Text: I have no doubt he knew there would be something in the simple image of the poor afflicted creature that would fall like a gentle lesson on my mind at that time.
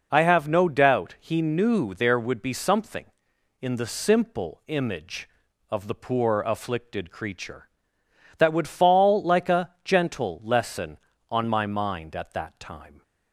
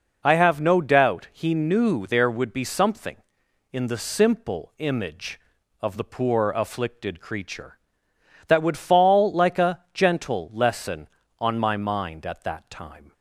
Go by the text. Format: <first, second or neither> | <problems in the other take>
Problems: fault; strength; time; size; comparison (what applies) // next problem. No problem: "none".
neither | none